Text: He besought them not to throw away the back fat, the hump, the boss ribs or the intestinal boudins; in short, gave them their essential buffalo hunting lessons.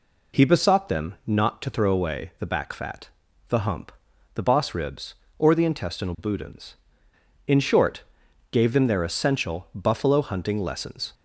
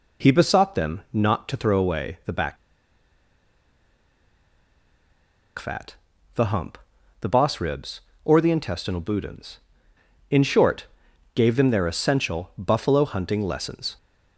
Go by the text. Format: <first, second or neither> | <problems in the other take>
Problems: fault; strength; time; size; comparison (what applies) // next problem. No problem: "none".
first | pauses between "back" and "fat"; strong; at 2.5 s; 3.0 s long